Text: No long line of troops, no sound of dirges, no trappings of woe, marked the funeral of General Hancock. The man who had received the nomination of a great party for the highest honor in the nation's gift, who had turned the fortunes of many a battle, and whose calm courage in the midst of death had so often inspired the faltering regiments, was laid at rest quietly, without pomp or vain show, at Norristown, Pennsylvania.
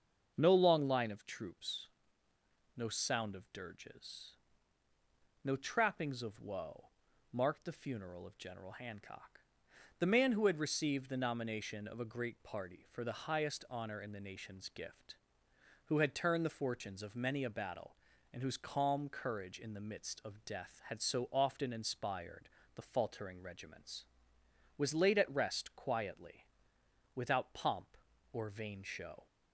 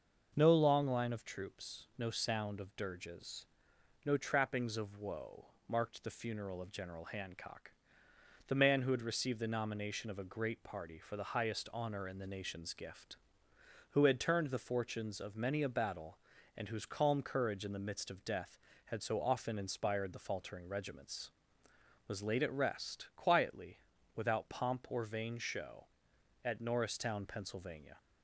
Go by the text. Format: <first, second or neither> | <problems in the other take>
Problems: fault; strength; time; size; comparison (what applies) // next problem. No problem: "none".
second | starts louder than the rest; until 1.3 s; 6.5 dB // pauses between "inspired" and "the"; slight; at 22.4 s; 0.26 s long // stops before "at Norristown Pennsylvania"; at 29.2 s